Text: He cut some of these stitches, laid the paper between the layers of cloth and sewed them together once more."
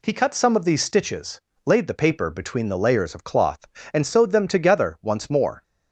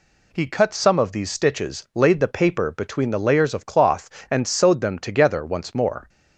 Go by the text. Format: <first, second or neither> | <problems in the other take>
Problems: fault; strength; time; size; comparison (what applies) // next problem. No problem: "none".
neither | none